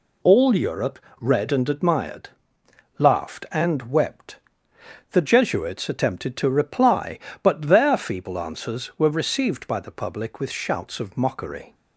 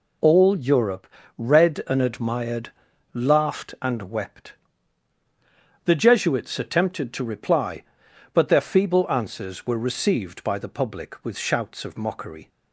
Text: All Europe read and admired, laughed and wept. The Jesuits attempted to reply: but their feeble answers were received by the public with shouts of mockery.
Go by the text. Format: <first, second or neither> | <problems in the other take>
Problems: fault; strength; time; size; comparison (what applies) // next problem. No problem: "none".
neither | pauses between "Europe" and "read"; slight; the same in both